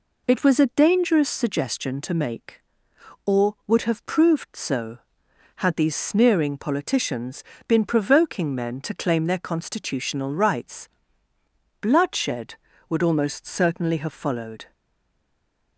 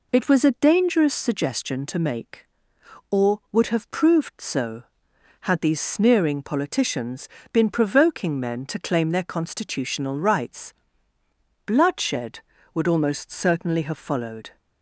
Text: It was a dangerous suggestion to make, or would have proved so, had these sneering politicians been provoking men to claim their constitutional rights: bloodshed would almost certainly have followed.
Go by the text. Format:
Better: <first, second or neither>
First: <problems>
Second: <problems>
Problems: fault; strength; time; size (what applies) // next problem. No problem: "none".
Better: second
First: pauses between "politicians" and "been"; slight; at 7.4 s; 0.24 s long // stays silent after the last word; from 14.7 s on; 1.0 s long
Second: pauses between "politicians" and "been"; slight; at 7.2 s; 0.24 s long